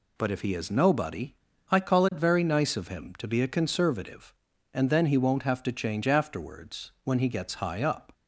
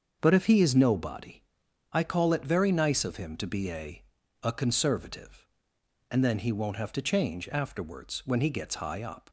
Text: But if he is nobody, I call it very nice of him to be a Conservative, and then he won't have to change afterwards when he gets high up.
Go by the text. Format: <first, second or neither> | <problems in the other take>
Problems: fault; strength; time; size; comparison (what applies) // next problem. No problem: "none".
first | starts louder than the rest; until 1.2 s; 6.5 dB // says "a" twice; at 4.4 s